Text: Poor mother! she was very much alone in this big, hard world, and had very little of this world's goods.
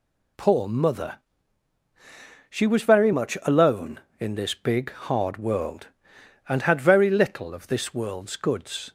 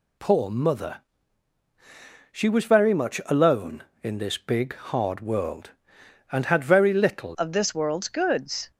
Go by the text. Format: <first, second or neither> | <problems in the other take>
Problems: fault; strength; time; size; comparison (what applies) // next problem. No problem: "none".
first | changes voice at "of"; from 7.3 s on; 1.4 s long